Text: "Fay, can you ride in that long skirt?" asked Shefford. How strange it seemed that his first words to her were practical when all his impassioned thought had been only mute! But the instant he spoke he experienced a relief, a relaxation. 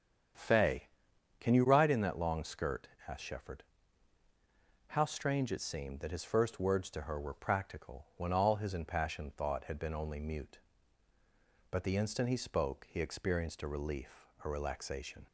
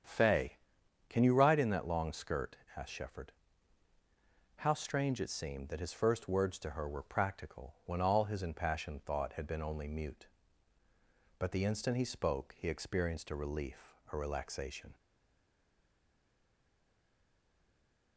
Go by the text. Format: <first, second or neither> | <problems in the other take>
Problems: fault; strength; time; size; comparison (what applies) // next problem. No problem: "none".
first | starts louder than the rest; strong; until 1.6 s; 8 dB; strong in the first // stays silent after the last word; strong; from 14.9 s on; 3.2 s long